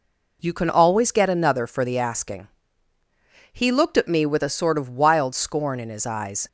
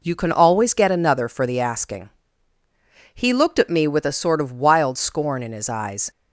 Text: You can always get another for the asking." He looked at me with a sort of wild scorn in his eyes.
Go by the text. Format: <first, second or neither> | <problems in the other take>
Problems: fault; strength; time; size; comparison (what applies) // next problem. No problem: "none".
neither | none